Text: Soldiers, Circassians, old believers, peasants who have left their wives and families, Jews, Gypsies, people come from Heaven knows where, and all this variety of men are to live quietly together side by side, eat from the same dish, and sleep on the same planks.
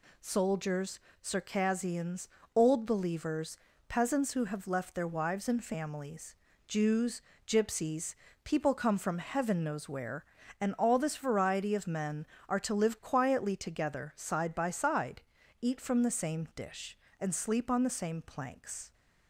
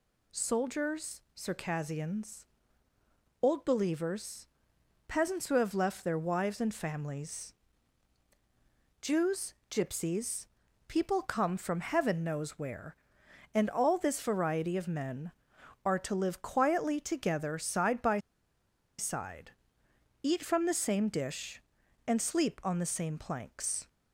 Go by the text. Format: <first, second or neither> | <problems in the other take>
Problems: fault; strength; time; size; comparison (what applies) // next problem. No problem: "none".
first | pauses between "by" and "side"; noticeable; at 18.1 s; 0.80 s long